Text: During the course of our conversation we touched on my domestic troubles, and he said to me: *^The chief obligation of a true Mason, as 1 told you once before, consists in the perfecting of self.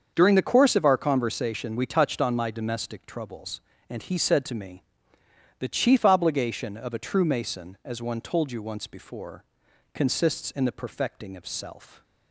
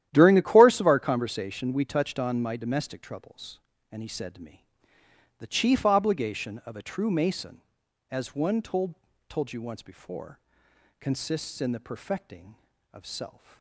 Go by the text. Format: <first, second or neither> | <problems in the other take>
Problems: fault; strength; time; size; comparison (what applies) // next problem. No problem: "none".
first | starts louder than the rest; strong; until 1.1 s; 12 dB; also in the first // says "told" twice; at 9.2 s